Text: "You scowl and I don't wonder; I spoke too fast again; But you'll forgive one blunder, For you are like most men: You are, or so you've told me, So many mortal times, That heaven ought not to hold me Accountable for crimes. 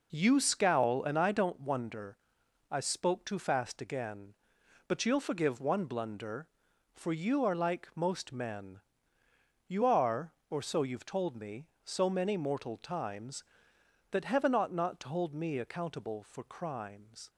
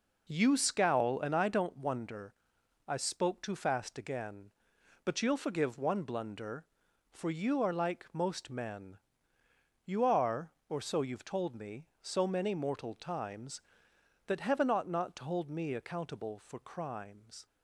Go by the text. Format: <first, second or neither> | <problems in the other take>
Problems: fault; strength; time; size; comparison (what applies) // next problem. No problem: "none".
neither | none